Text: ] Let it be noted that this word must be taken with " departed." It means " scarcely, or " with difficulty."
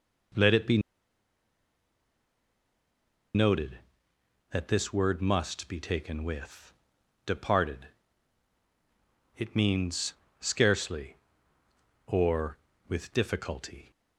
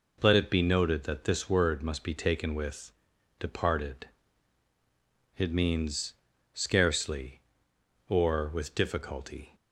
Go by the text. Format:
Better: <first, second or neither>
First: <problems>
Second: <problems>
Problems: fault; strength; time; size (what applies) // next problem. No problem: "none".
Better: second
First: pauses between "be" and "noted"; strong; at 0.7 s; 2.5 s long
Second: none